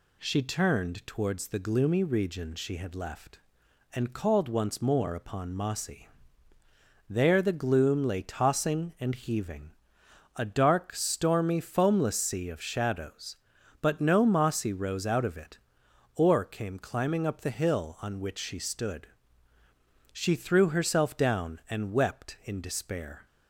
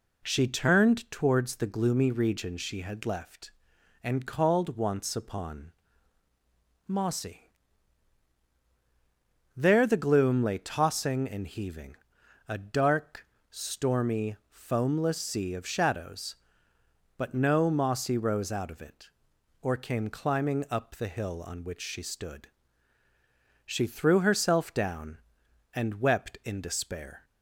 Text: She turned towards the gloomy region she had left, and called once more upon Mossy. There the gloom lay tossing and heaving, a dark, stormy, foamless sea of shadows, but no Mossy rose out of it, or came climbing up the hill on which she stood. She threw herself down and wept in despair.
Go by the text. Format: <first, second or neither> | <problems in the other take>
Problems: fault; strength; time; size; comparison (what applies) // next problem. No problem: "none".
first | skips "more"; at 5.1 s // pauses between "upon" and "Mossy"; at 5.7 s; 1.1 s long